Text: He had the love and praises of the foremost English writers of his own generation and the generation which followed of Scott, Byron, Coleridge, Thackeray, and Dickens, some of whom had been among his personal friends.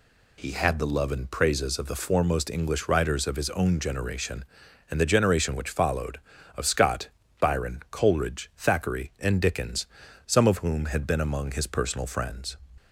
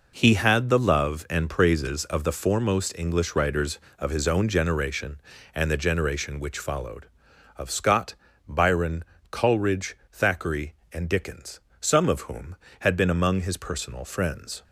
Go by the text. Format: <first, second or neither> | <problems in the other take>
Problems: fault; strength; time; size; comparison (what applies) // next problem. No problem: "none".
neither | none